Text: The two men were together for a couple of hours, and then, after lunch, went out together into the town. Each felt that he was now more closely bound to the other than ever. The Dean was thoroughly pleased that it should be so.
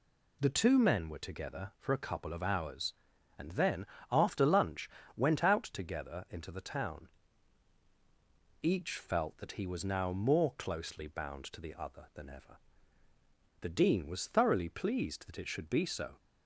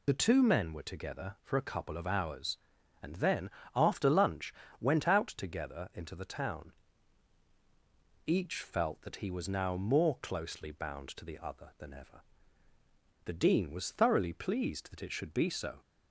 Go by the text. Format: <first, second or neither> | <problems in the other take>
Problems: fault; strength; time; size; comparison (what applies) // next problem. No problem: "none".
first | loses the start of "The"; at 0.0 s; 30 ms